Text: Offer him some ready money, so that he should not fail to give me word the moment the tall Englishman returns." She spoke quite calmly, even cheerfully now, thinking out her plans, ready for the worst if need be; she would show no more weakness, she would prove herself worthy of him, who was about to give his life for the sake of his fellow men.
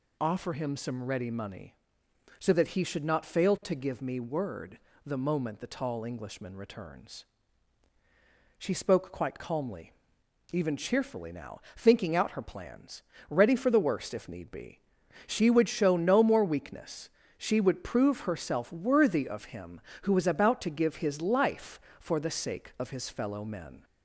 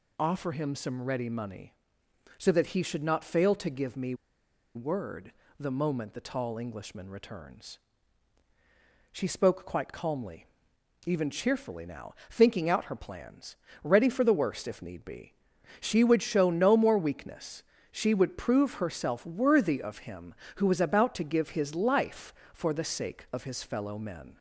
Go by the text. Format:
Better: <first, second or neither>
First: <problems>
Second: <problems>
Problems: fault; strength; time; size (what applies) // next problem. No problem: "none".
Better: first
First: pauses between "word" and "the"; slight; at 4.7 s; 0.28 s long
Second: pauses between "me" and "word"; noticeable; at 4.1 s; 0.62 s long // pauses between "word" and "the"; slight; at 5.3 s; 0.28 s long